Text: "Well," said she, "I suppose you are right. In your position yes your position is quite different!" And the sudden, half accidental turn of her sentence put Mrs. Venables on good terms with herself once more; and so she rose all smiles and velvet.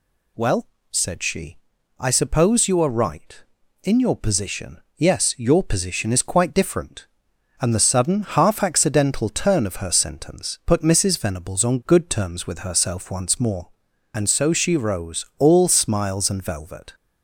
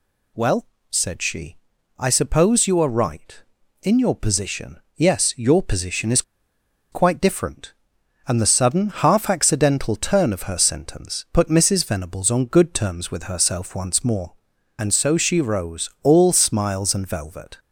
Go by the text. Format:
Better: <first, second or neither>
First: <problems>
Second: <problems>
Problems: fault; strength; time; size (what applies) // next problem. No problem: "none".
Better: first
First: pauses between "position" and "yes"; slight; at 4.8 s; 0.16 s long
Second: pauses between "position" and "yes"; slight; at 4.7 s; 0.16 s long // pauses between "is" and "quite"; noticeable; at 6.2 s; 0.70 s long